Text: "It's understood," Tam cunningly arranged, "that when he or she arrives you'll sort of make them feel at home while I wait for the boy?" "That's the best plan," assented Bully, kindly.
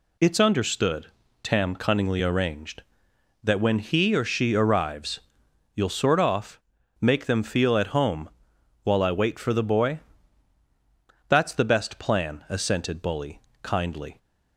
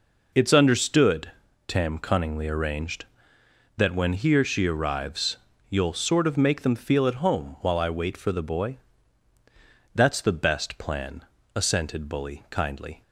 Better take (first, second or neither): second